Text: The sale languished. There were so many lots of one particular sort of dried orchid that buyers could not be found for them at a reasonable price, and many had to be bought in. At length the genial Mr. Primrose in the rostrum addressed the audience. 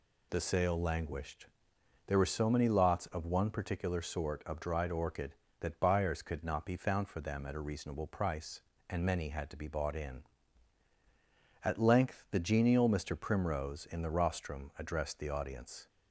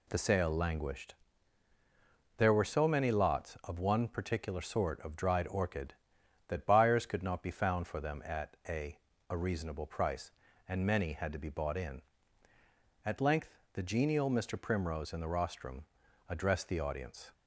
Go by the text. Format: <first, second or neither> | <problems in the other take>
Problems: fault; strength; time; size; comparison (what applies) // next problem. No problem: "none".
first | says "a" twice; at 9.2 s // pauses between "length" and "the"; slight; at 13.5 s; 0.16 s long // pauses between "rostrum" and "addressed"; at 15.8 s; 0.42 s long